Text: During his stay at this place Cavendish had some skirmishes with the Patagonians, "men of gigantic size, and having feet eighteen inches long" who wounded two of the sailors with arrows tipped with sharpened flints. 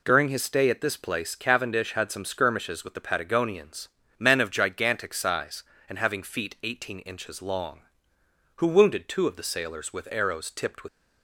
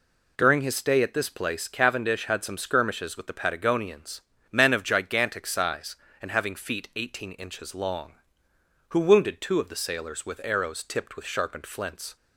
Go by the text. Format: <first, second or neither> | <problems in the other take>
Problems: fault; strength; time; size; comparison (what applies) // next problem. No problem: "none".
second | stops before "sharpened flints"; at 10.8 s